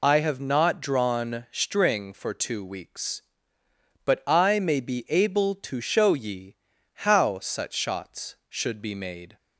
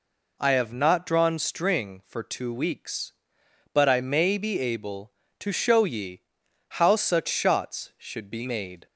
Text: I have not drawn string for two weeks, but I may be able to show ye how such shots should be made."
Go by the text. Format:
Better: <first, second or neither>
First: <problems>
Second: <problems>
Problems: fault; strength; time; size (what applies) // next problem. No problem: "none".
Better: second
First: loses the start of "I"; at 0.0 s; 45 ms // pauses between "ye" and "how"; at 6.5 s; 0.38 s long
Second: pauses between "ye" and "how"; noticeable; at 6.2 s; 0.48 s long